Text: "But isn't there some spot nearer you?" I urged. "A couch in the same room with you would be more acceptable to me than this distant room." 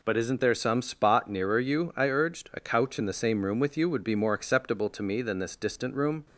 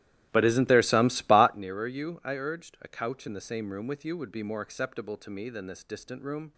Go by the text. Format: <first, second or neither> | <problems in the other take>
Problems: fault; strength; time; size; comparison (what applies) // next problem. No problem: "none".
first | starts louder than the rest; strong; until 1.6 s; 14 dB